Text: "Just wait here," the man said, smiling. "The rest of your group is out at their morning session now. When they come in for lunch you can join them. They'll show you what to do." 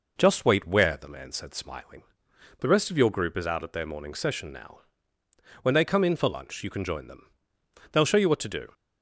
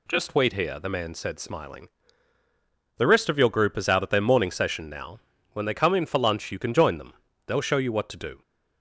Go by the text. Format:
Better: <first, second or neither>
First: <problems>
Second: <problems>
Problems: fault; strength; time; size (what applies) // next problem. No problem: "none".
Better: second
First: says "where" for "here"; at 0.6 s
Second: none